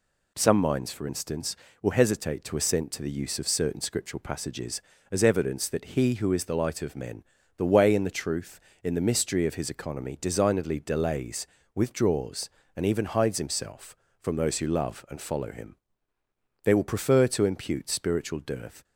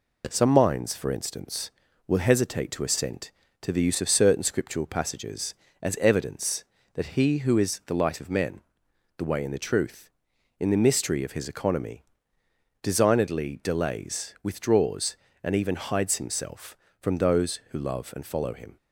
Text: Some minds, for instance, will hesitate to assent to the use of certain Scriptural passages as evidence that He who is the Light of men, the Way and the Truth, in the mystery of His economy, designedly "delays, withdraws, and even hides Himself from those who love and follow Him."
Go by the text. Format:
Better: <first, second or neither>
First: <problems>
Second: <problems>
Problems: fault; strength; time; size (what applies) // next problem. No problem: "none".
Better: second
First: goes on to say "They will prefer to impute spiritual dearth"; strong; from 16.6 s on; 2.1 s long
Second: none